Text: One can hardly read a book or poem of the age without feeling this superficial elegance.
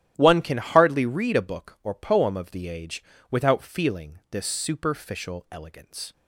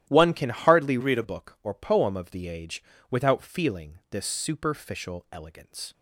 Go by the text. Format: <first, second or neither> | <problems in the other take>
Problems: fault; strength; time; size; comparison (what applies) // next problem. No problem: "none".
first | starts louder than the rest; strong; until 1.1 s; 12.5 dB; strong in the first // changes voice from "read" to "a"; from 0.9 to 1.2 s; 0.3 s long // pauses between "age" and "without"; slight; at 2.8 s; 0.30 s long; slight in the first